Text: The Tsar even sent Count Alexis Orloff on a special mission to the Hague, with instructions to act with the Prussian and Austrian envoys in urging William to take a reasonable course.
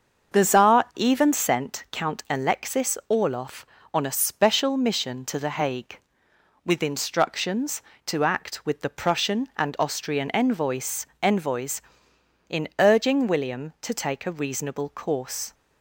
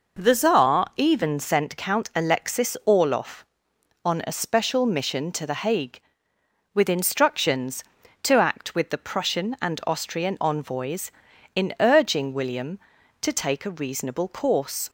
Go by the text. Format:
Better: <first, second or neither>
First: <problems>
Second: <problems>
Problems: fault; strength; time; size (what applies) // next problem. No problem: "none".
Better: second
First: starts louder than the rest; until 1.4 s; 7 dB // says "envoys" twice; at 11.2 s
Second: none